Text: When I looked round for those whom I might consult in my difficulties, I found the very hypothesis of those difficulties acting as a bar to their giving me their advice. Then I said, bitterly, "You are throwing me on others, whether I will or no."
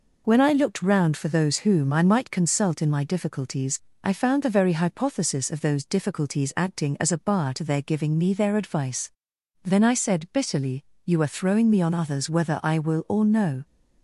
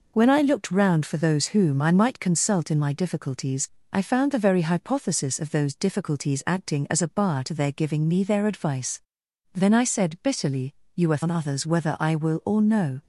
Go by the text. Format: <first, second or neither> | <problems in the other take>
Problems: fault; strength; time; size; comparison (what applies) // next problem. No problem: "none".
first | skips "throwing me"; at 11.2 s